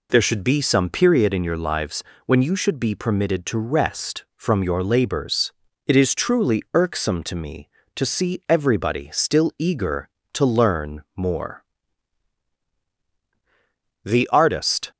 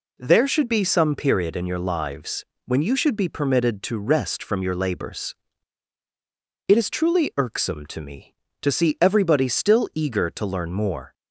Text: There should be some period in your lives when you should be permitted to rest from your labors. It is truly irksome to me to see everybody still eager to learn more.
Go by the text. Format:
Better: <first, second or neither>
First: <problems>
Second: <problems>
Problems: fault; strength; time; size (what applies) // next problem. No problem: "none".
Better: second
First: pauses between "lives" and "when"; slight; at 2.0 s; 0.24 s long // goes on to say "The artist"; noticeable; from 14.0 s on; 0.88 s long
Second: pauses between "lives" and "when"; slight; at 2.4 s; 0.22 s long